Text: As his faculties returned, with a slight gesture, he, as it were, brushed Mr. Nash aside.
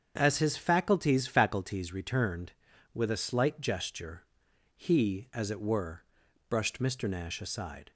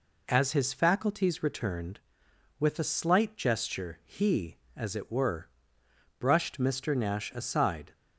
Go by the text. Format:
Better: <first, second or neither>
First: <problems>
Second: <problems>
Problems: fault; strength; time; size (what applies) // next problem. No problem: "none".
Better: second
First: starts louder than the rest; strong; until 1.1 s; 7.5 dB // says "faculties" twice; at 1.2 s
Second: none